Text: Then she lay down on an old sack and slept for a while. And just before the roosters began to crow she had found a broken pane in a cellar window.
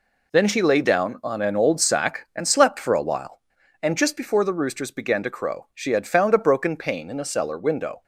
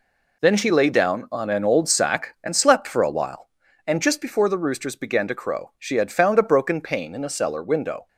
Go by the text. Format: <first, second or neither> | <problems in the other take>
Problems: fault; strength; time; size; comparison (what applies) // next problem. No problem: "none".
neither | none